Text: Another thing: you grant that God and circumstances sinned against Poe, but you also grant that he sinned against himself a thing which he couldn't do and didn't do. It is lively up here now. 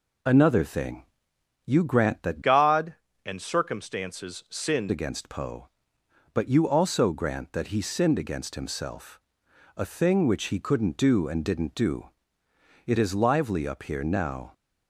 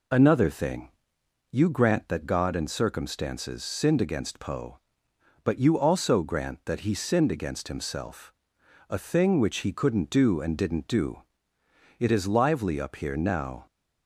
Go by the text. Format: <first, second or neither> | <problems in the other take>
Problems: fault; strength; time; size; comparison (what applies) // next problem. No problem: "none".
second | changes voice from "God" to "sinned"; from 2.4 to 4.9 s; 2.5 s long // pauses between "himself" and "a"; noticeable; at 9.1 s; 0.58 s long; noticeable in the second